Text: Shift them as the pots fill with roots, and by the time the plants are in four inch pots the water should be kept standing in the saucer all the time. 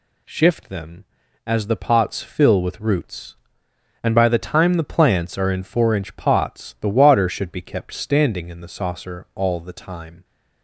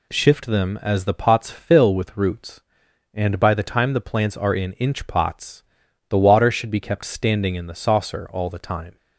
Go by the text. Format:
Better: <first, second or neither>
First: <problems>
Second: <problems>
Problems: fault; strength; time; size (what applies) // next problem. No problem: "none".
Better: first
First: none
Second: skips "four"; at 4.7 s // pauses between "pots" and "the"; noticeable; at 5.6 s; 0.46 s long